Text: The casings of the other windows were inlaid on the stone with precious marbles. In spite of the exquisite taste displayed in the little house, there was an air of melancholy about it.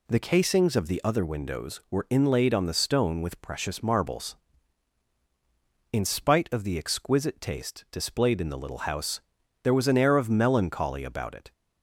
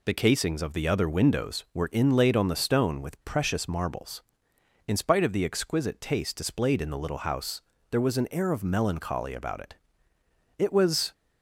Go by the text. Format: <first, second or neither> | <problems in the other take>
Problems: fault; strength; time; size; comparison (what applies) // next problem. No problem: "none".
first | goes on to say "It was"; from 10.5 s on; 0.54 s long